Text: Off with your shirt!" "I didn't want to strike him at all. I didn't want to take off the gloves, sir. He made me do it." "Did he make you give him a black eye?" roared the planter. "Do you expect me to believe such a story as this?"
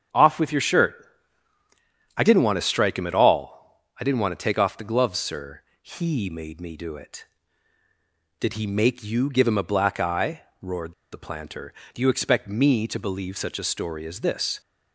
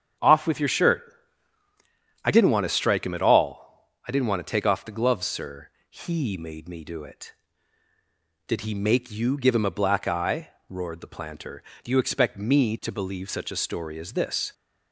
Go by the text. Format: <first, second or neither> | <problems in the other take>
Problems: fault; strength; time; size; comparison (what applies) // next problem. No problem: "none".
second | starts louder than the rest; strong; until 2.2 s; 7.5 dB; strong in the second // pauses between "roared" and "the"; slight; at 10.9 s; 0.18 s long